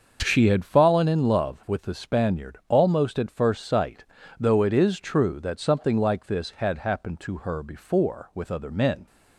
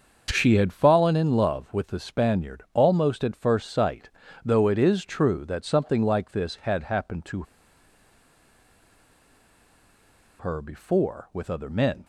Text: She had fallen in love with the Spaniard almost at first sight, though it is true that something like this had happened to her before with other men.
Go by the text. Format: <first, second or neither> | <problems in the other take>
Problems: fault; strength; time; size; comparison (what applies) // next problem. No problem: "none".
first | starts louder than the rest; until 1.3 s; 6.5 dB; also in the first // pauses between "to" and "her"; strong; at 7.4 s; 3.0 s long